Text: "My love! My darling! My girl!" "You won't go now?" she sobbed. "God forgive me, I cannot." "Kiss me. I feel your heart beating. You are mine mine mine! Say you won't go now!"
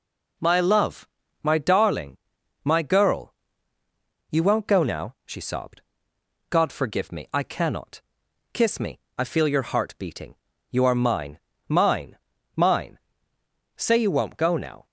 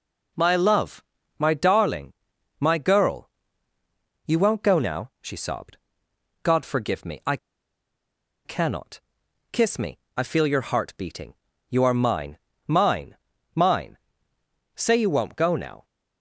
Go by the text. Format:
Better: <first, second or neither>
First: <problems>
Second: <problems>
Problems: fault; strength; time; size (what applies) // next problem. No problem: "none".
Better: first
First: pauses between "mine" and "mine"; slight; at 11.3 s; 0.28 s long // pauses between "mine" and "mine"; at 12.1 s; 0.38 s long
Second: pauses between "I" and "cannot"; at 7.3 s; 1.0 s long // pauses between "mine" and "mine"; slight; at 12.3 s; 0.28 s long // pauses between "mine" and "mine"; at 13.1 s; 0.38 s long